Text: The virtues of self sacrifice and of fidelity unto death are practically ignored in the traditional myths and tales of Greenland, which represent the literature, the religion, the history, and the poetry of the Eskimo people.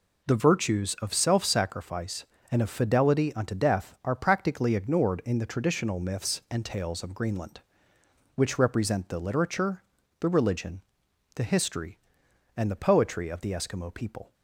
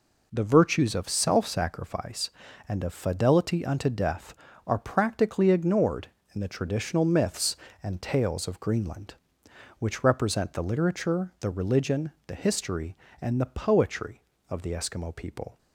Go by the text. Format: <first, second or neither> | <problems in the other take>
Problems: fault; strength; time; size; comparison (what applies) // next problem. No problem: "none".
neither | none